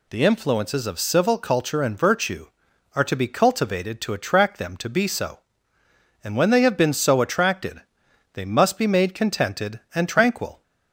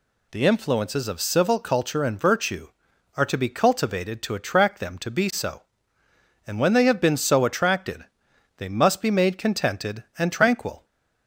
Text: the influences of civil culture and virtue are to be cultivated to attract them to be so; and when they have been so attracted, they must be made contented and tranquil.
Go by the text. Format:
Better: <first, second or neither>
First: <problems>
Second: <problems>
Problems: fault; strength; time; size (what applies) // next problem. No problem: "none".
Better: neither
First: none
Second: none